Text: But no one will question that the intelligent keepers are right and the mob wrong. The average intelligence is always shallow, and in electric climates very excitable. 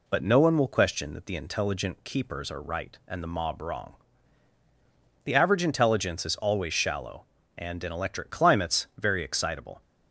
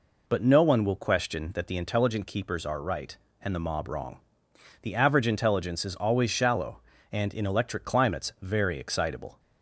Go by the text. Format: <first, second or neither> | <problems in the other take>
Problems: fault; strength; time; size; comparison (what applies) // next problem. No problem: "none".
neither | none